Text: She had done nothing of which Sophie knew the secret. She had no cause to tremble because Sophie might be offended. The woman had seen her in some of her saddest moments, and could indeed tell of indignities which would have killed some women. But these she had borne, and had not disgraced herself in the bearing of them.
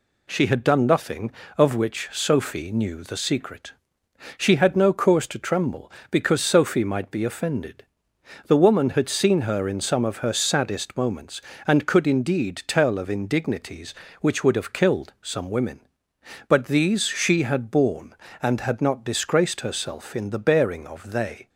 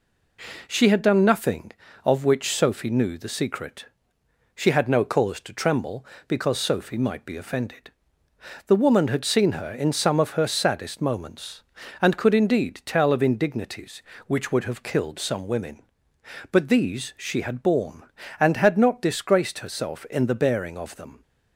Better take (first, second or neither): second